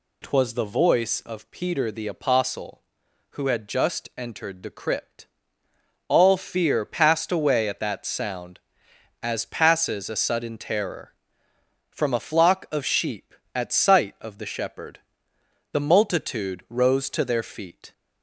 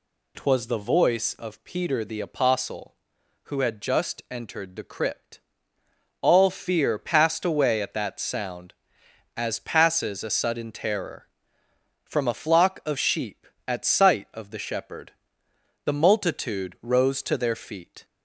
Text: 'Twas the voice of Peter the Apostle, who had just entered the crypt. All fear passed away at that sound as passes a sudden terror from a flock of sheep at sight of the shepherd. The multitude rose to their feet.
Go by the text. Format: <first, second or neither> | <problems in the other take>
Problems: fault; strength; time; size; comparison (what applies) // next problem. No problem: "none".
neither | none